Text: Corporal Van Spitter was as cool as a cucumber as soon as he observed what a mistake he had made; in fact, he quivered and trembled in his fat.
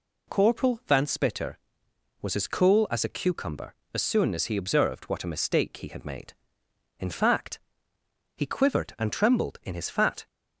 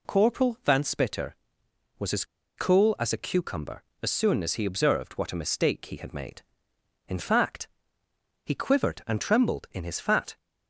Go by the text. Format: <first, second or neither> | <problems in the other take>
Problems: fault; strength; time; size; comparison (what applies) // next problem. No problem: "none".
first | pauses between "as" and "cool"; slight; at 2.2 s; 0.33 s long